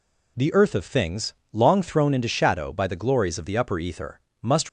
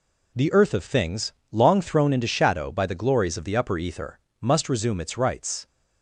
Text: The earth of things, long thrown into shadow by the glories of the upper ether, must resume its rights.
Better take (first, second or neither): second